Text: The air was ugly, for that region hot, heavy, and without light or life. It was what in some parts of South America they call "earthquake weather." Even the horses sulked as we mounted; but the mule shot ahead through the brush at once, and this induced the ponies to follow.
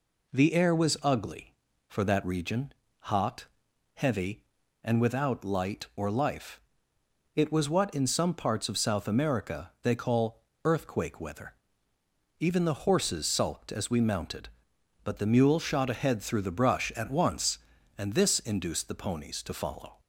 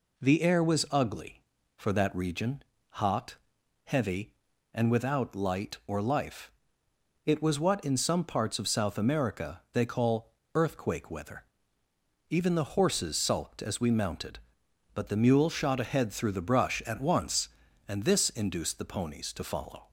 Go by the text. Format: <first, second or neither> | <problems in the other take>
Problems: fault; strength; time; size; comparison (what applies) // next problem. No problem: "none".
neither | pauses between "region" and "hot"; slight; the same in both // pauses between "call" and "earthquake"; slight; the same in both